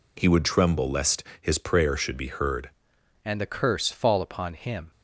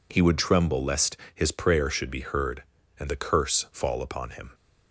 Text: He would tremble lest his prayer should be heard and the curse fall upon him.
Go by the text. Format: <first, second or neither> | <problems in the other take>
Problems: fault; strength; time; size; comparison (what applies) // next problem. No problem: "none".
second | pauses between "lest" and "his"; slight; at 1.2 s; 0.18 s long; slight in the second // changes voice at "and"; from 3.2 s on; 1.7 s long